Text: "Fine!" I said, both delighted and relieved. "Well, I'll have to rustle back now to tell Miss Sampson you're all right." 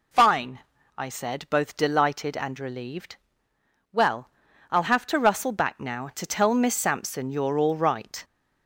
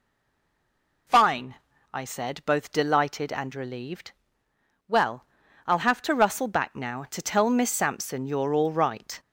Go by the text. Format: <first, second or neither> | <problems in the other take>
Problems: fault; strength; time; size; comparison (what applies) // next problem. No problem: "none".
first | stays silent before the first word; until 1.0 s; 1.0 s long